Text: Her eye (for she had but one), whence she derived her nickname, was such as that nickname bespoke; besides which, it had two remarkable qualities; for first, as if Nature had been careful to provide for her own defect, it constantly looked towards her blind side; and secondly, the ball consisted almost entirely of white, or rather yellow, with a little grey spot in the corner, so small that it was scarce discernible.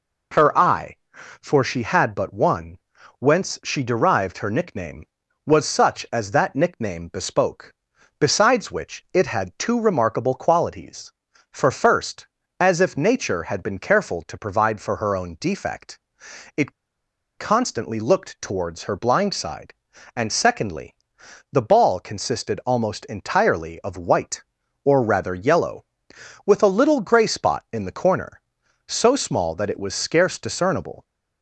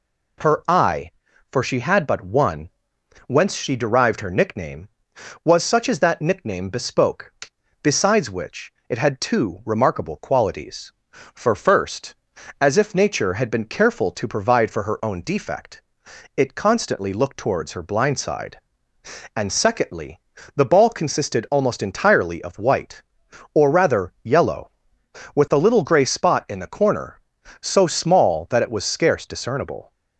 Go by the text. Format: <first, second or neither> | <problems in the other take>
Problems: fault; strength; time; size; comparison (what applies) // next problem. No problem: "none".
second | pauses between "it" and "constantly"; noticeable; at 16.7 s; 0.65 s long